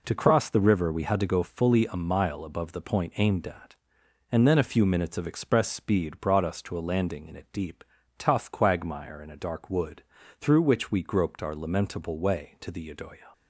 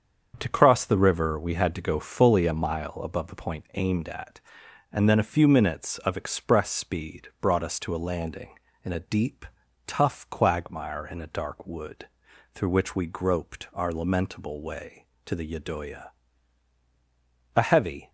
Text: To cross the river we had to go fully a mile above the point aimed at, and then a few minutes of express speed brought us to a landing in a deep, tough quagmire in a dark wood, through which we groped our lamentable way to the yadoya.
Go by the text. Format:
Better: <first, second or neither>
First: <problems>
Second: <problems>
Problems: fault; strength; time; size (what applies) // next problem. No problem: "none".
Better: first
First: none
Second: starts louder than the rest; strong; until 1.3 s; 7.5 dB // goes on to say "A heavy"; from 17.5 s on; 0.54 s long